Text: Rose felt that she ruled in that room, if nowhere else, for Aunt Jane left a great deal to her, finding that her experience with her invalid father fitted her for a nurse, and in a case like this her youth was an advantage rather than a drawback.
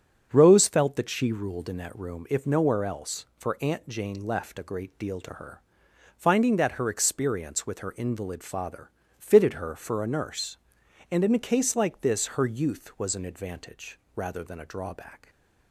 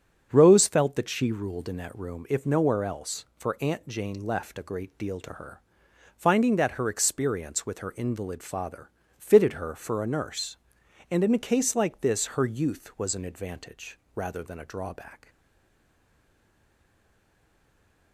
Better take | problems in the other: first | starts louder than the rest; until 1.3 s; 7 dB; also in the first // pauses between "father" and "fitted"; slight; at 8.9 s; 0.26 s long; slight in the first // pauses between "advantage" and "rather"; slight; at 13.9 s; 0.16 s long; slight in the first // stays silent after the last word; strong; from 15.2 s on; 2.9 s long

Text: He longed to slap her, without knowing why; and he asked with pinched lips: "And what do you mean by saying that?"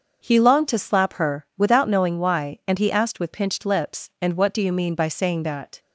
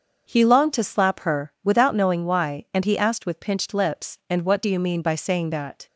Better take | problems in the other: neither | starts louder than the rest; the same in both

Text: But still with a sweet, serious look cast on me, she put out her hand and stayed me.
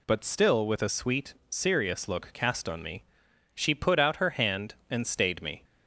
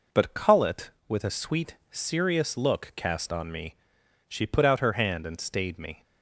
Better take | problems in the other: first | says "cullet" for "still"; at 0.3 s

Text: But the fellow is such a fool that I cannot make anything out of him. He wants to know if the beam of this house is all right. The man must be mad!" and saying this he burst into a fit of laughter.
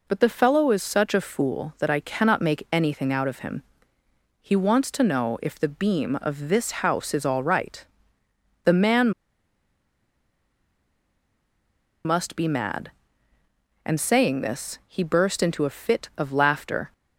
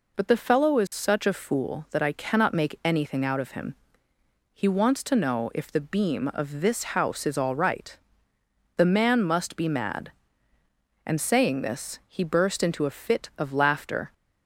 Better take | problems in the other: second | pauses between "man" and "must"; strong; at 9.1 s; 2.9 s long

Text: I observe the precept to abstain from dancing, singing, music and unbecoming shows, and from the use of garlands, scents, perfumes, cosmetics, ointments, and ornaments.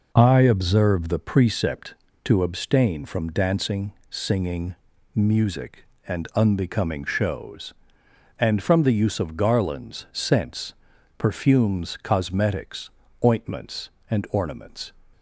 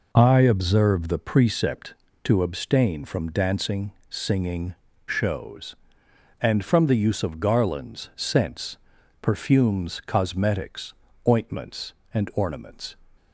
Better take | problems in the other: first | skips "music and unbecoming"; at 4.9 s

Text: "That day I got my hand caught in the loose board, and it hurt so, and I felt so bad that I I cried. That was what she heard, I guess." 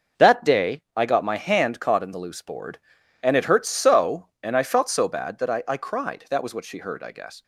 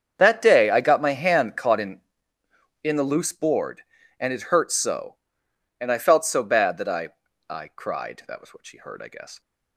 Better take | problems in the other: first | starts louder than the rest; strong; until 1.1 s; 7.5 dB // says "in" twice; at 2.8 s // pauses between "I" and "I"; at 7.1 s; 0.40 s long

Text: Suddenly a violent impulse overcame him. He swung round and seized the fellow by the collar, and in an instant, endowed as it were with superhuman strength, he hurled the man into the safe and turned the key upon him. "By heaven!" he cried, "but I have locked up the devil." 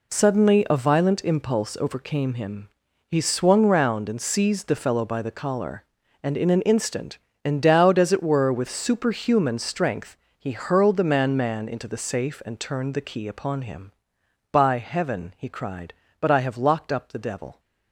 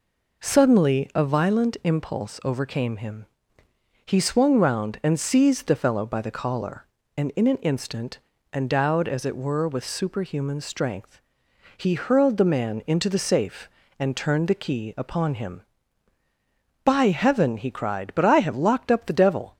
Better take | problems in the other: second | says "man" twice; at 11.3 s

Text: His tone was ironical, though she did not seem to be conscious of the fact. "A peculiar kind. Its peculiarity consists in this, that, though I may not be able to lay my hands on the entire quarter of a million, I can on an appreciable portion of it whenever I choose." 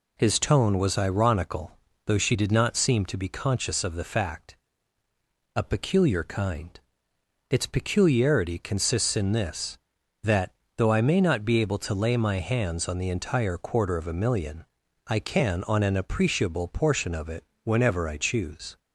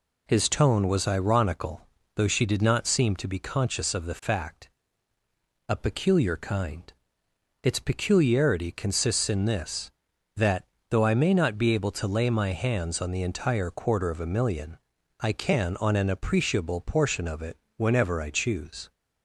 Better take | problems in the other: neither | pauses between "it" and "whenever"; slight; the same in both

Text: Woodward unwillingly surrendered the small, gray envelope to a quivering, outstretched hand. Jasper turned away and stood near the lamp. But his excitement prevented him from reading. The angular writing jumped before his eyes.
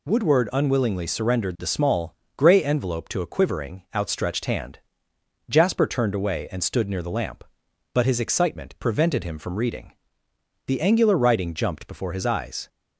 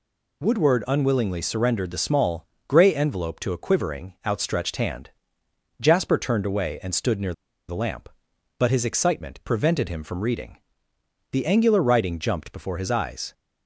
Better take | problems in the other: first | pauses between "near" and "the"; slight; at 7.3 s; 0.35 s long

